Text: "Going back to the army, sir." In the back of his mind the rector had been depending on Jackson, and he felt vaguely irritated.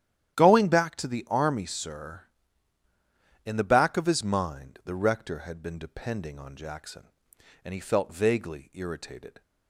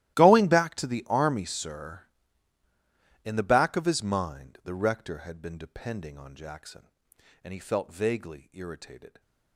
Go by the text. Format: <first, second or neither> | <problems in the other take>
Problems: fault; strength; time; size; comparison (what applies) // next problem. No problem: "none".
first | gets quieter; strong; throughout; 21 dB // starts louder than the rest; strong; until 1.2 s; 15 dB; strong in the first